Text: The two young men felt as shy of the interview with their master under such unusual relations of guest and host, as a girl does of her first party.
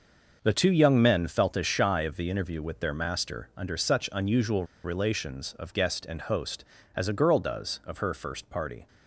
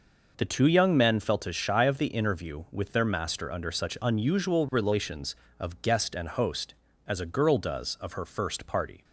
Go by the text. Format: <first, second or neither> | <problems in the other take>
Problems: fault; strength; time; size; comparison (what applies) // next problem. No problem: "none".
second | starts louder than the rest; noticeable; until 1.4 s; 6 dB // pauses between "unusual" and "relations"; slight; at 4.6 s; 0.20 s long